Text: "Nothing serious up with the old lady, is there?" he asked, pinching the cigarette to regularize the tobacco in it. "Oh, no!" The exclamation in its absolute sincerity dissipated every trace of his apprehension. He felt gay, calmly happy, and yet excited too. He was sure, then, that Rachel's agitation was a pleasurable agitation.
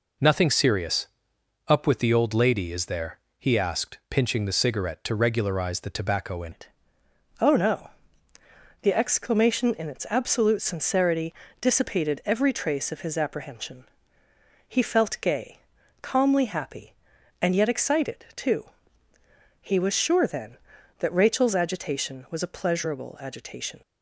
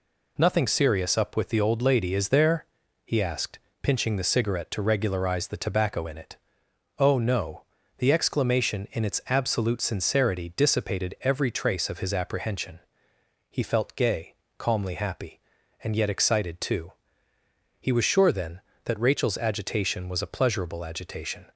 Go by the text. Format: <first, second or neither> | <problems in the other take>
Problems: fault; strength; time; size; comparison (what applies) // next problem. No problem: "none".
second | pauses between "serious" and "up"; noticeable; at 1.0 s; 0.58 s long // changes voice at "it"; from 6.5 s on; 17.3 s long // pauses between "sincerity" and "dissipated"; slight; at 11.3 s; 0.26 s long